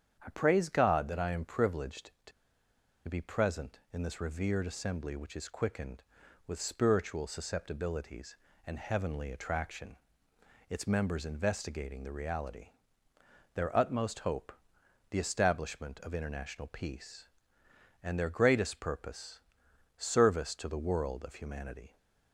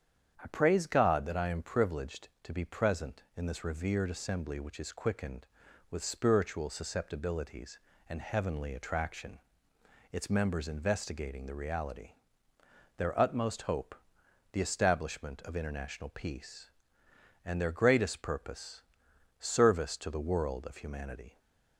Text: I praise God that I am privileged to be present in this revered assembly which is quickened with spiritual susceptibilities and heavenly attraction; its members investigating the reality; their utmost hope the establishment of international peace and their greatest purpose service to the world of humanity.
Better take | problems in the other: second | starts louder than the rest; strong; until 1.2 s; 8.5 dB; strong in the second // pauses between "to" and "be"; noticeable; at 2.3 s; 0.76 s long // pauses between "hope" and "the"; noticeable; at 14.5 s; 0.58 s long; noticeable in the second // pauses between "purpose" and "service"; noticeable; at 19.4 s; 0.56 s long; noticeable in the second

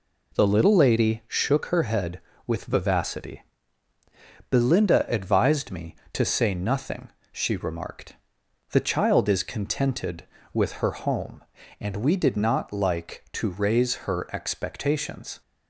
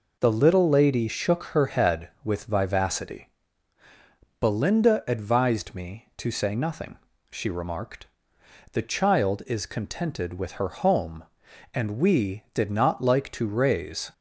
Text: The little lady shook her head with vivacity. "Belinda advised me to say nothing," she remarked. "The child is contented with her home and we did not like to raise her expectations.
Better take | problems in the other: first | stops before "her expectations"; at 14.1 s

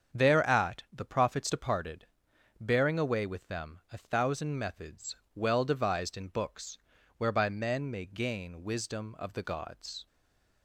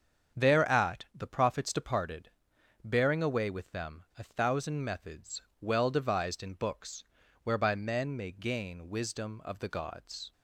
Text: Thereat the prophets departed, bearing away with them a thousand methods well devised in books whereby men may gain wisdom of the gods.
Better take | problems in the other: second | starts louder than the rest; strong; until 1.2 s; 7 dB; strong in the second // pauses between "methods" and "well"; slight; at 5.1 s; 0.20 s long; slight in the second // pauses between "books" and "whereby"; at 6.7 s; 0.40 s long; also in the second // stays silent after the last word; slight; from 10.0 s on; 0.6 s long

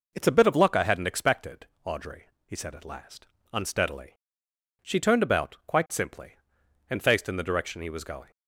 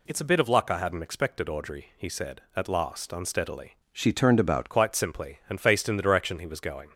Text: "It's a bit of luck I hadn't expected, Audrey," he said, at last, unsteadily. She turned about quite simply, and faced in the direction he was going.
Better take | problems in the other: first | changes voice from "She" to "about"; from 3.9 to 4.7 s; 0.8 s long

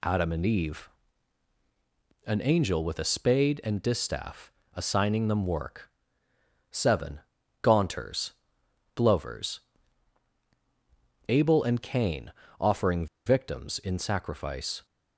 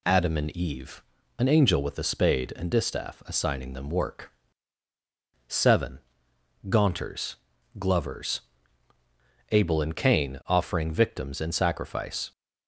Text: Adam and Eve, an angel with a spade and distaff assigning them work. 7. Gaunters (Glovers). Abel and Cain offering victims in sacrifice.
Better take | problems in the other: second | pauses between "distaff" and "assigning"; slight; at 4.5 s; 0.24 s long // pauses between "Cain" and "offering"; slight; at 12.3 s; 0.28 s long // pauses between "offering" and "victims"; slight; at 13.0 s; 0.20 s long

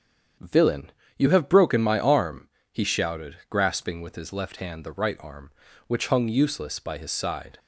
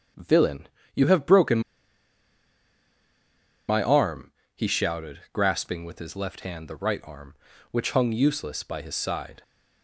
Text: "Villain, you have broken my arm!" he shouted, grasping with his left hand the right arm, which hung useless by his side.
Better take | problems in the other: first | starts louder than the rest; strong; until 1.4 s; 8 dB; strong in the first // pauses between "broken" and "my"; strong; at 1.6 s; 2.0 s long

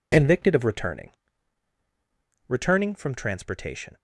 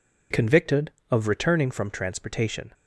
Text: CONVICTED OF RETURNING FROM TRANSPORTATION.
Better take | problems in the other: second | says "RETURNING" twice; at 2.4 s

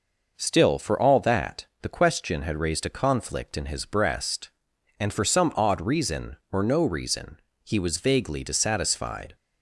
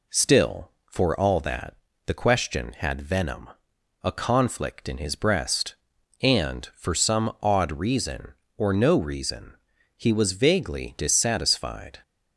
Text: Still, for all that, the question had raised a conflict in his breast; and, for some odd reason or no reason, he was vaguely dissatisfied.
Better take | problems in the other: first | says "venom" for "raised"; at 3.0 s

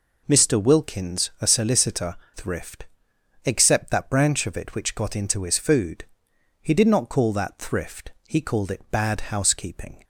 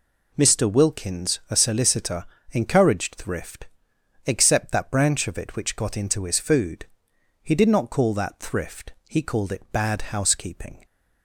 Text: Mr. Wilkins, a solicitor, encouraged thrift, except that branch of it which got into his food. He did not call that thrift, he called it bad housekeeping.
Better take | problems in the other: second | skips "encouraged"; at 2.2 s

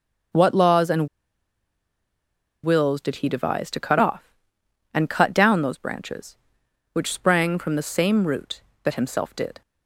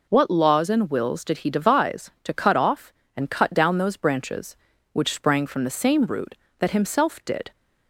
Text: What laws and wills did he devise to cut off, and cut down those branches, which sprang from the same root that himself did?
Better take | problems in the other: second | starts louder than the rest; until 2.9 s; 7 dB // pauses between "and" and "wills"; strong; at 1.0 s; 1.5 s long

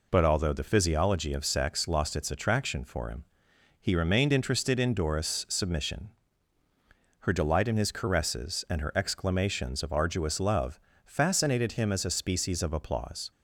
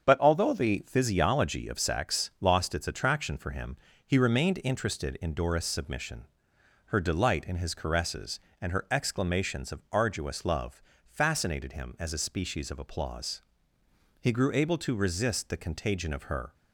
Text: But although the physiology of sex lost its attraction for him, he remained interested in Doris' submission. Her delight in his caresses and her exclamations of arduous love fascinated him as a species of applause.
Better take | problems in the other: first | starts louder than the rest; strong; until 1.1 s; 7.5 dB // pauses between "love" and "fascinated"; slight; at 10.8 s; 0.26 s long; slight in the first // goes on to say "He grew able to resist the contagion of her"; strong; from 14.1 s on; 2.3 s long

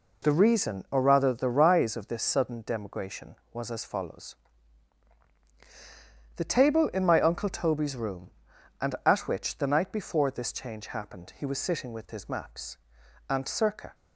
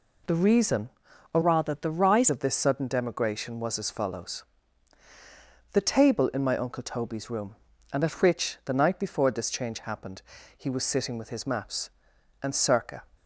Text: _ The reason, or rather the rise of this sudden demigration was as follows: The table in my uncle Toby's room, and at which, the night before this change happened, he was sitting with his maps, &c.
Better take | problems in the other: first | changes voice from "rather" to "rise"; from 1.4 to 2.2 s; 0.8 s long

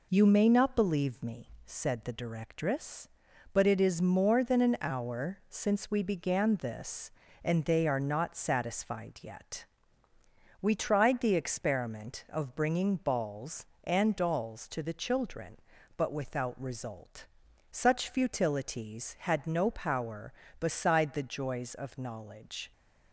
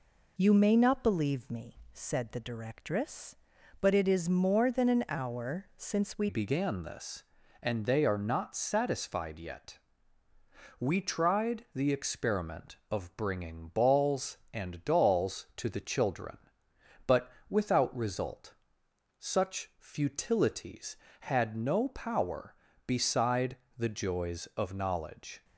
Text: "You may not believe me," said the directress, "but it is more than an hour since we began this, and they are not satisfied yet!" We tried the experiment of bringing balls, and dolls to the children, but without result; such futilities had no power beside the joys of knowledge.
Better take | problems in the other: first | changes voice at "began"; from 6.2 s on; 19.2 s long // pauses between "but" and "without"; slight; at 17.3 s; 0.18 s long // pauses between "beside" and "the"; slight; at 23.5 s; 0.22 s long

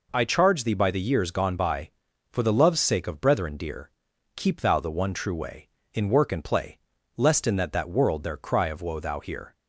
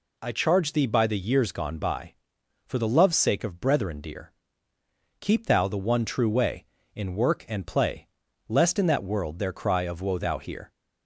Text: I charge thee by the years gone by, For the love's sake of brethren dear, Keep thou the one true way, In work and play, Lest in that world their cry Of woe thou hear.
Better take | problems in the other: second | says "that" twice; at 7.7 s

